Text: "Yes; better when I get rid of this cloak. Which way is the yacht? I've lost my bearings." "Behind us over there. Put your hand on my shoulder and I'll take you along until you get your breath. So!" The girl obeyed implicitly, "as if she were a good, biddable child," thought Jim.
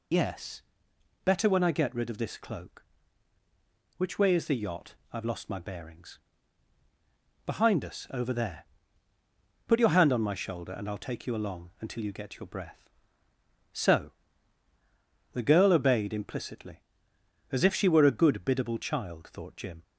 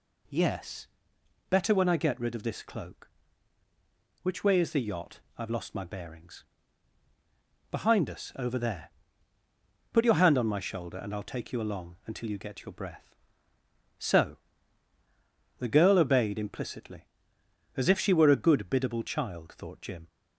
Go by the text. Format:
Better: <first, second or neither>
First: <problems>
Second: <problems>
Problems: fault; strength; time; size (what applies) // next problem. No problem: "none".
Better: second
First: loses the start of "Yes"; at 0.1 s; 115 ms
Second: none